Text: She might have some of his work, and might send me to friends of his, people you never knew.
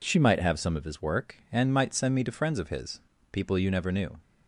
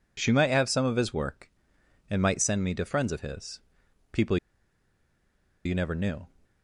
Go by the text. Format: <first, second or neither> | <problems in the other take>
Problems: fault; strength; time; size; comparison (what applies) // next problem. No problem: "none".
first | pauses between "people" and "you"; strong; at 4.3 s; 1.2 s long